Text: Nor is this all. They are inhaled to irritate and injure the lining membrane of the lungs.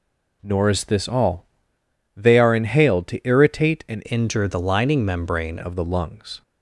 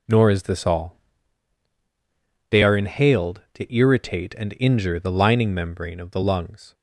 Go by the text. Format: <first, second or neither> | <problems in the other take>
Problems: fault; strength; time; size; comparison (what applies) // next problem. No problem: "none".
second | changes voice from "injure" to "membrane"; from 4.1 to 5.5 s; 1.4 s long